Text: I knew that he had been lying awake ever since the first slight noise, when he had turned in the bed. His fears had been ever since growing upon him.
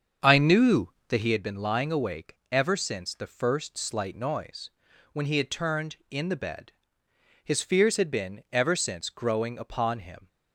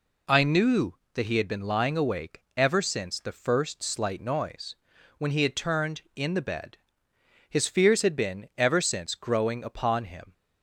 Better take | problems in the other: second | starts louder than the rest; until 1.4 s; 7 dB

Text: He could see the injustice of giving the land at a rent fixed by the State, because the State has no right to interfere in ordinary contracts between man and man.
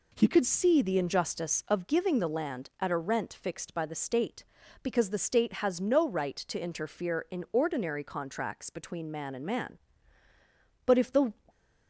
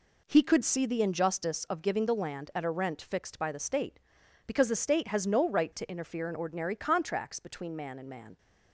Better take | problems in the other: second | goes on to say "But if the"; slight; from 10.8 s on; 0.48 s long

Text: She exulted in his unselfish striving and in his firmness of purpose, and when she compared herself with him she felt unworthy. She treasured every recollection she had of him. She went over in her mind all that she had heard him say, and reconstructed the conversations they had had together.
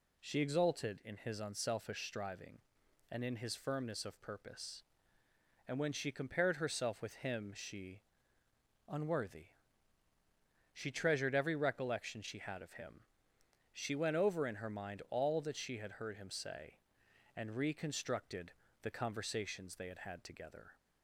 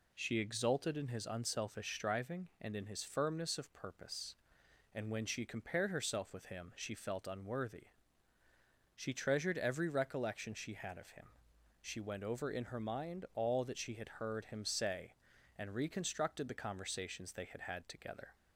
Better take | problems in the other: second | skips "felt"; at 8.4 s // pauses between "reconstructed" and "the"; slight; at 18.5 s; 0.28 s long

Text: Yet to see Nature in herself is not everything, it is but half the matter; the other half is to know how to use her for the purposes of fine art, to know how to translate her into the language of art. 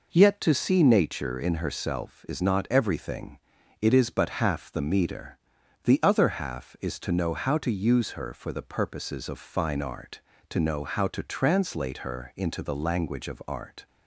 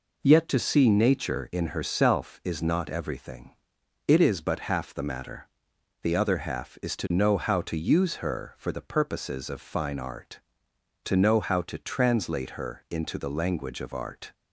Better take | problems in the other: second | says "meter" for "matter"; at 4.8 s

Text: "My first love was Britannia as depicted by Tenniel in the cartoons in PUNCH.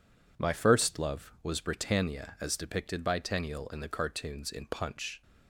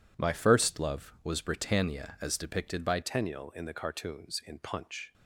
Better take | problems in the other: first | changes voice at "Tenniel"; from 3.0 s on; 2.1 s long

